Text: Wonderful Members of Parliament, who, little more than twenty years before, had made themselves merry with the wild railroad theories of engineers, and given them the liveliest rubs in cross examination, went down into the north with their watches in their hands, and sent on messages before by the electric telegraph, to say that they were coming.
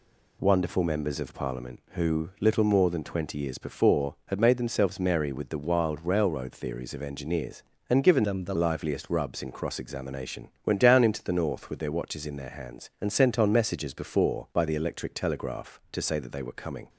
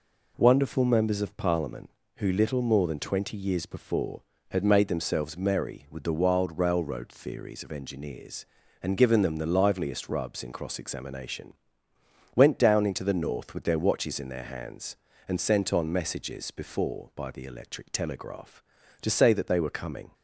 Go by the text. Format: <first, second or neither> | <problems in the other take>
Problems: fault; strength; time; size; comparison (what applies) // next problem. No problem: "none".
second | changes voice from "them" to "the"; from 8.2 to 8.5 s; 0.3 s long